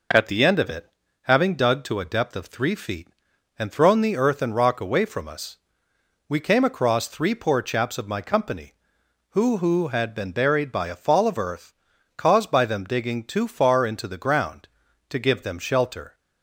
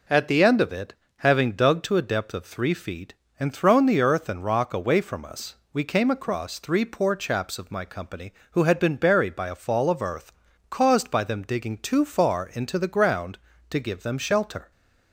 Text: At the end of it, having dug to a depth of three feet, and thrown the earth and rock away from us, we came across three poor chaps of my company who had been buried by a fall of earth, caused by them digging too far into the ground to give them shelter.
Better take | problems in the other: second | says "who" twice; at 9.5 s

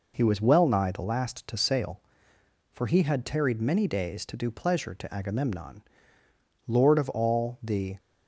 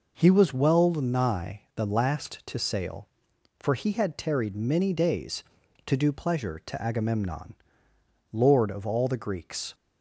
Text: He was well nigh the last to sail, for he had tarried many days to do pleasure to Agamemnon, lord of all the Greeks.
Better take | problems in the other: second | stops before "Greeks"; at 7.9 s

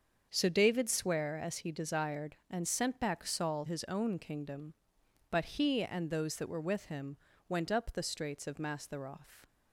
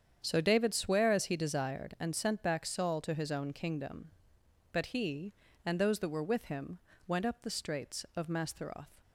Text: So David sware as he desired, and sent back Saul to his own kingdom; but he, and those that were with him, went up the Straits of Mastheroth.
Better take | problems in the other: second | starts louder than the rest; until 1.3 s; 7 dB; strong in the second // skips "to"; at 3.6 s

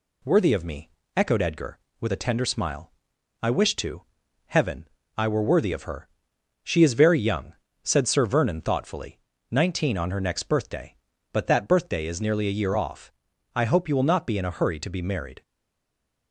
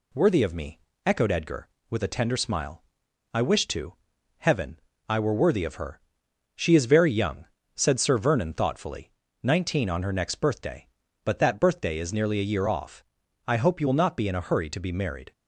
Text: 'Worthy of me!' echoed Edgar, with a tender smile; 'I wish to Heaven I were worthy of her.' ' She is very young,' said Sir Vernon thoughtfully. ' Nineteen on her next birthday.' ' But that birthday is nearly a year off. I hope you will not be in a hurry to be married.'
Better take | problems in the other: second | pauses between "to" and "Heaven"; noticeable; at 4.0 s; 0.46 s long; noticeable in the second // pauses between "Heaven" and "I"; slight; at 4.8 s; 0.30 s long; slight in the second // stays silent after the last word; slight; from 15.4 s on; 0.9 s long

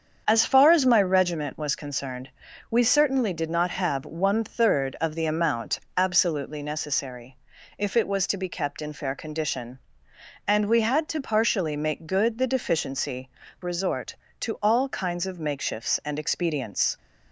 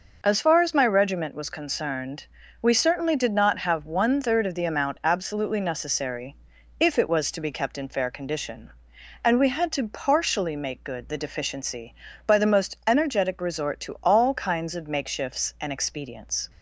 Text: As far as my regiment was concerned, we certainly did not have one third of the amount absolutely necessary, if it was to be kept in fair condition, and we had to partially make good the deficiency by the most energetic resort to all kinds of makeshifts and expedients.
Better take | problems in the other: second | starts louder than the rest; strong; until 1.2 s; 7.5 dB // pauses between "amount" and "absolutely"; slight; at 5.7 s; 0.20 s long // skips "by the most energetic"; at 13.4 s

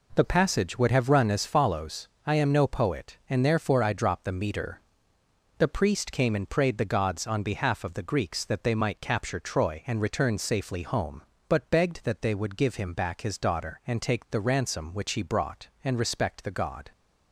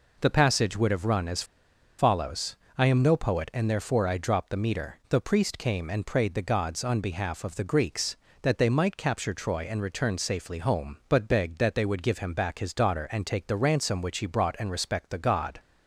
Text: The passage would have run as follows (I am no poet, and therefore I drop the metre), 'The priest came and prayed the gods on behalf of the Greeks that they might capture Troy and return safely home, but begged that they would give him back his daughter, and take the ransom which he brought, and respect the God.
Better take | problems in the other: first | pauses between "as" and "follows"; noticeable; at 1.4 s; 0.55 s long

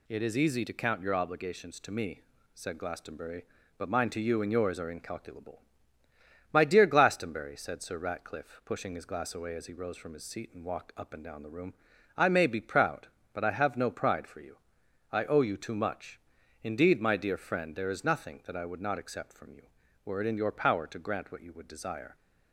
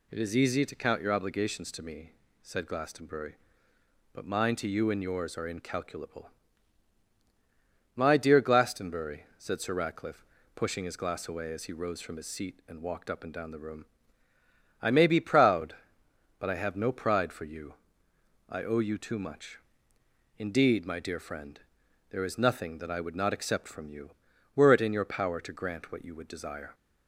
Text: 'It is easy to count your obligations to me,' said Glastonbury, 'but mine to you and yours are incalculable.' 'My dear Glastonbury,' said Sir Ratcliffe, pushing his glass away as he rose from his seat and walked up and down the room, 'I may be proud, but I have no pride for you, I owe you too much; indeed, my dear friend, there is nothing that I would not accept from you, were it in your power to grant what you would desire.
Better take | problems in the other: neither | none

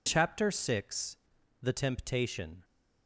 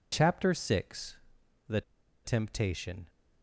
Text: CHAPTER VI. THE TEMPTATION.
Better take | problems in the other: first | pauses between "THE" and "TEMPTATION"; at 1.8 s; 0.43 s long

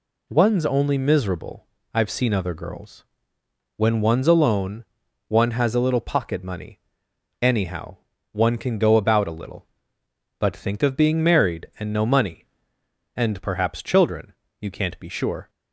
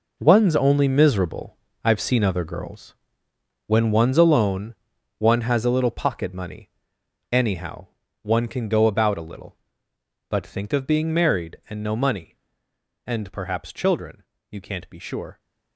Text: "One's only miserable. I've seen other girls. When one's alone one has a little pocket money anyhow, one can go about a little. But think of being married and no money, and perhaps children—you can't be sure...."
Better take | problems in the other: first | gets quieter; strong; throughout; 11.5 dB // pauses between "alone" and "one"; at 4.7 s; 0.44 s long; also in the first // pauses between "money" and "anyhow"; noticeable; at 6.6 s; 0.62 s long; noticeable in the first

